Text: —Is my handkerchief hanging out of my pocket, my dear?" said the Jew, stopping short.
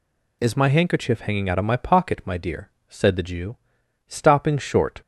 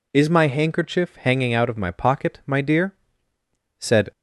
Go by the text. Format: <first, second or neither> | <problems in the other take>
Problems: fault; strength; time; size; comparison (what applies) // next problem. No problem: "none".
first | stops before "the Jew stopping short"; at 4.1 s